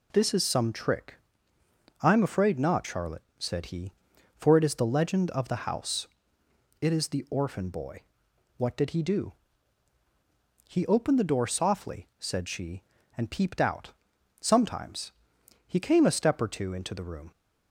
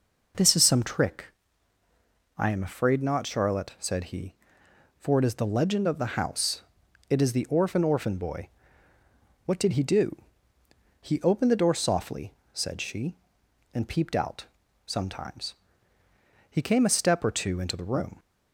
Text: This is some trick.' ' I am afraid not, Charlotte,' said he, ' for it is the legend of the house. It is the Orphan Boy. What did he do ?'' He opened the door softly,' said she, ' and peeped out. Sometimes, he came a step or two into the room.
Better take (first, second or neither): first